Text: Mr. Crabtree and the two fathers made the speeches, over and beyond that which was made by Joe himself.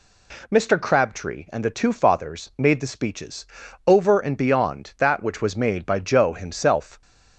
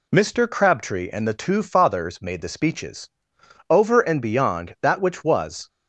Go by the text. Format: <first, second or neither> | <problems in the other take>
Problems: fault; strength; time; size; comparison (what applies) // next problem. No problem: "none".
first | stops before "made by Joe himself"; at 5.6 s